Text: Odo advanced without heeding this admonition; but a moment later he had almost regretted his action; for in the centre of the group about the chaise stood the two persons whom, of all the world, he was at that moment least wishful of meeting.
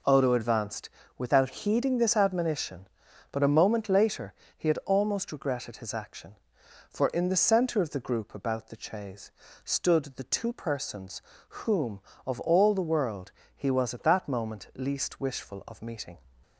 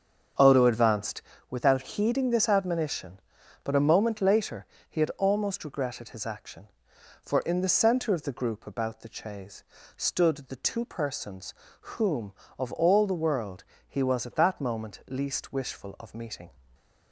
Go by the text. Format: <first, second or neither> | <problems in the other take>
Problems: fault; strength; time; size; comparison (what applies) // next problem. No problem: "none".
first | starts louder than the rest; until 1.5 s; 6.5 dB // pauses between "advanced" and "without"; slight; at 1.2 s; 0.26 s long; slight in the first // pauses between "later" and "he"; slight; at 4.6 s; 0.20 s long; slight in the first // pauses between "chaise" and "stood"; slight; at 9.6 s; 0.34 s long; slight in the first // pauses between "persons" and "whom"; at 11.5 s; 0.42 s long; also in the first // stays silent after the last word; slight; from 16.5 s on; 0.6 s long